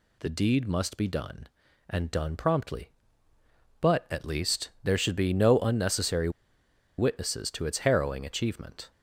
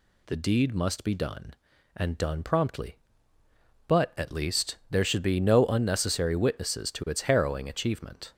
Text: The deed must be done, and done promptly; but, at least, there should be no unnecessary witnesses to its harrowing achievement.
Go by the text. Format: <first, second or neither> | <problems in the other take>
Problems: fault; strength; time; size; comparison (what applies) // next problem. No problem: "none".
second | pauses between "unnecessary" and "witnesses"; noticeable; at 6.3 s; 0.68 s long